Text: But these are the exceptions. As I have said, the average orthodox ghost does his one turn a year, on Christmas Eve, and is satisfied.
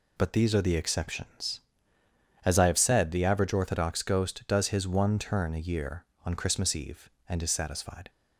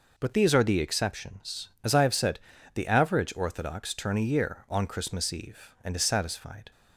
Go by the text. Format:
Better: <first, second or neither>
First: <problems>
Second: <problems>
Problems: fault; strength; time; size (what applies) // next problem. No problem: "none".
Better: first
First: none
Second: skips "ghost does his one"; at 3.9 s